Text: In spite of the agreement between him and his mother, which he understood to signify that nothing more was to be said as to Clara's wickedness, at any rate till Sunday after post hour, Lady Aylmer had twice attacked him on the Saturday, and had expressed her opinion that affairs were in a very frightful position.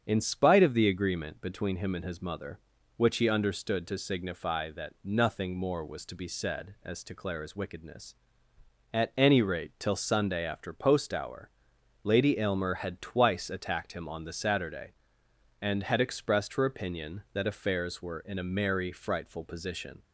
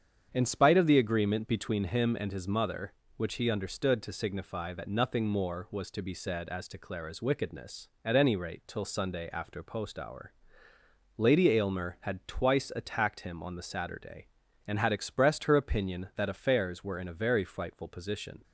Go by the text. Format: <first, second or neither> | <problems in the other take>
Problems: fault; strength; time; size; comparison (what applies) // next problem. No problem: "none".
second | starts louder than the rest; strong; until 1.0 s; 7.5 dB; strong in the second // says "merry" for "very"; at 18.4 s